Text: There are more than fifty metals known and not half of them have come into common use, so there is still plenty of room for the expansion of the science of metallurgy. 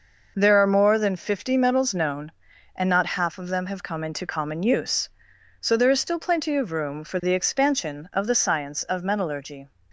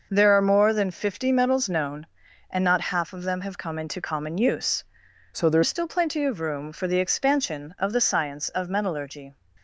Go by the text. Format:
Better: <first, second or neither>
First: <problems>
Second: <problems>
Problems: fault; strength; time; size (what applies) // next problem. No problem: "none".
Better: first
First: none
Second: changes voice from "so" to "there"; from 5.3 to 5.6 s; 0.3 s long